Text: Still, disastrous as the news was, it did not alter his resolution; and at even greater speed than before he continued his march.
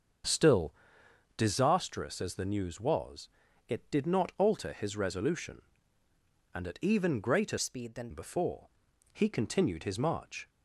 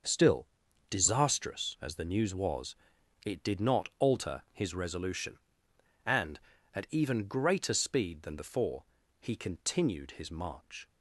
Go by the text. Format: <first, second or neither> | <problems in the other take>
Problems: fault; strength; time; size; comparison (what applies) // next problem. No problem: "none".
second | starts louder than the rest; until 1.9 s; 7 dB; also in the second // changes voice from "speed" to "than"; from 7.5 to 8.0 s; 0.5 s long // pauses between "before" and "he"; at 8.6 s; 0.44 s long; also in the second